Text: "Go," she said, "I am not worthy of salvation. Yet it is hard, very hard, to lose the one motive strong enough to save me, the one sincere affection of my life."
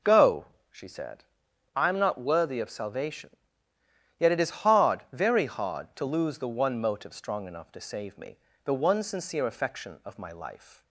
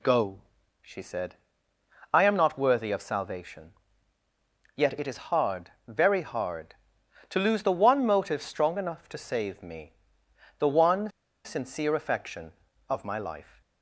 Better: first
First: none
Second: pauses between "one" and "sincere"; slight; at 11.1 s; 0.34 s long

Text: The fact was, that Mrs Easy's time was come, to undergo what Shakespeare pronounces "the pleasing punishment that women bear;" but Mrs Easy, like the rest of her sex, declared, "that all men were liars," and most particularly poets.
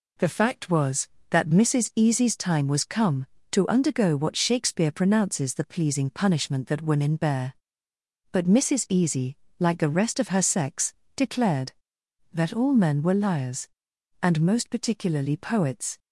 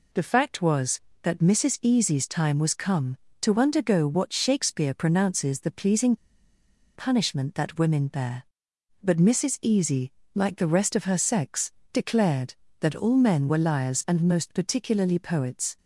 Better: first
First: none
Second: pauses between "pleasing" and "punishment"; noticeable; at 6.1 s; 0.79 s long

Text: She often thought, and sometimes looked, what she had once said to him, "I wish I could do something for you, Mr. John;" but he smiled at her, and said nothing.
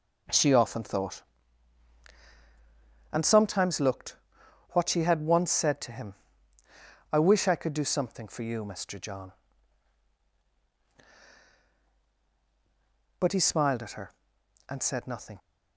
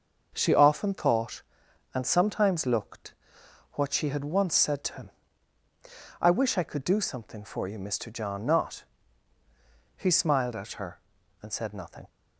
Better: first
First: none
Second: starts louder than the rest; until 1.3 s; 6.5 dB // says "not" for "but"; at 8.4 s

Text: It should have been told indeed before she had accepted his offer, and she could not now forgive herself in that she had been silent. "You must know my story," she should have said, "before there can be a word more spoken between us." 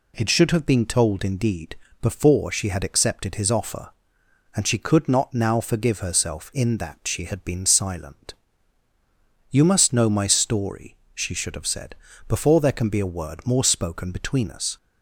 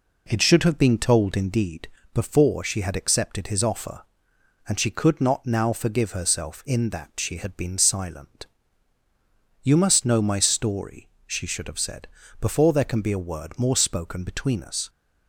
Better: first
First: pauses between "indeed" and "before"; slight; at 1.7 s; 0.26 s long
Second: starts louder than the rest; until 1.8 s; 4 dB // pauses between "indeed" and "before"; slight; at 1.8 s; 0.26 s long

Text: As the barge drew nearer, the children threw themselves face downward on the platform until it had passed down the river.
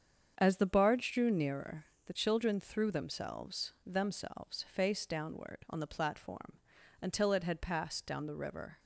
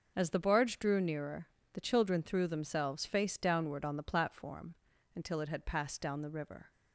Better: second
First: starts louder than the rest; strong; until 1.4 s; 7.5 dB // says "themselves" twice; at 3.8 s // pauses between "platform" and "until"; at 6.5 s; 0.44 s long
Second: pauses between "platform" and "until"; at 4.7 s; 0.40 s long

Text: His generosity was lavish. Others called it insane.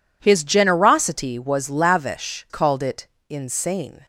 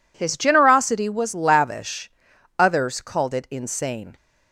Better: second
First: skips "Others"; at 2.4 s // pauses between "it" and "insane"; slight; at 3.0 s; 0.22 s long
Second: none

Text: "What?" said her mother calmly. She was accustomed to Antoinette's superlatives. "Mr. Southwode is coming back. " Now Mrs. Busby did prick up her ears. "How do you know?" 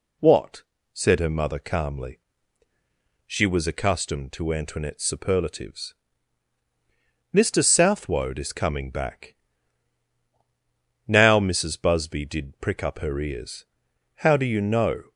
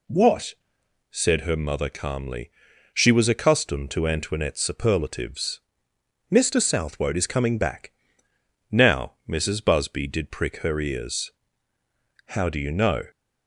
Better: first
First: none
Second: skips "up"; at 10.5 s

